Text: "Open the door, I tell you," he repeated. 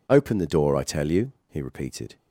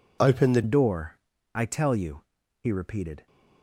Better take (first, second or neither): first